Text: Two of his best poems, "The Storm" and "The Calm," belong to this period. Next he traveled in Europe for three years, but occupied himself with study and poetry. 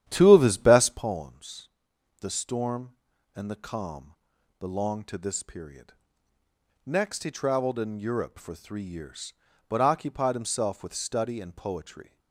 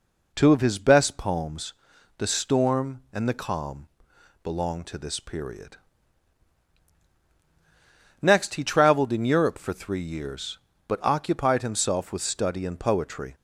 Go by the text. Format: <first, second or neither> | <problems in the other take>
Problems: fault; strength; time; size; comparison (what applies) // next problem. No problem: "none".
second | starts louder than the rest; strong; until 1.2 s; 10.5 dB